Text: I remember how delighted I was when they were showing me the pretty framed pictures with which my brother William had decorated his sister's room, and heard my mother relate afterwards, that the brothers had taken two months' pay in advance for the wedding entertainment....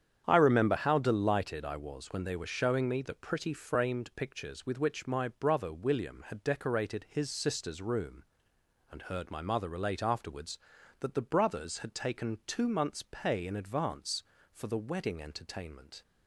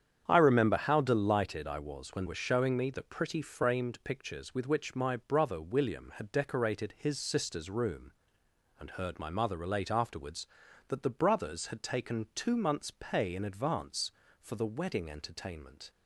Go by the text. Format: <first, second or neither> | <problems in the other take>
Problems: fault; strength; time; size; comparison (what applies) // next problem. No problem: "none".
first | starts louder than the rest; strong; until 1.2 s; 8.5 dB; strong in the first // skips "they"; at 2.2 s